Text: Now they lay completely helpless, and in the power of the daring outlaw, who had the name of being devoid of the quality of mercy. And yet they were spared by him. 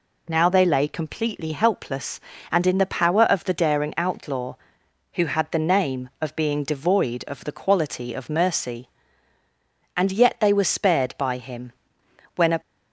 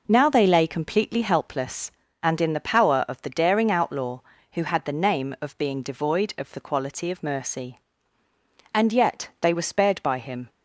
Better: second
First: goes on to say "When a"; slight; from 12.3 s on; 0.24 s long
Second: none

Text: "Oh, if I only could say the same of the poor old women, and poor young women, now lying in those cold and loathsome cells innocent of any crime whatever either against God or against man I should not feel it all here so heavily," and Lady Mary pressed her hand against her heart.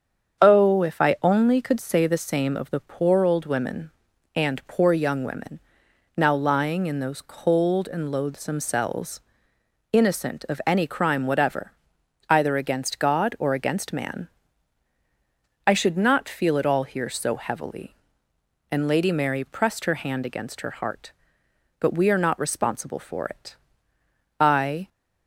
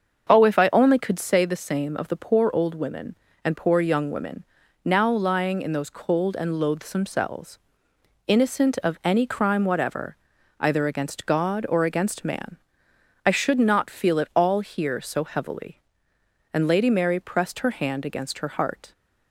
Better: second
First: starts louder than the rest; strong; until 1.4 s; 7.5 dB // pauses between "cells" and "innocent"; noticeable; at 9.2 s; 0.72 s long // pauses between "whatever" and "either"; noticeable; at 11.7 s; 0.58 s long // pauses between "man" and "I"; strong; at 14.2 s; 1.3 s long // goes on to say "But we are not responsible for it I"; strong; from 21.8 s on; 3.0 s long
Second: starts louder than the rest; until 1.3 s; 6.5 dB // pauses between "cells" and "innocent"; noticeable; at 7.5 s; 0.68 s long // pauses between "whatever" and "either"; at 10.1 s; 0.42 s long // pauses between "man" and "I"; noticeable; at 12.5 s; 0.68 s long

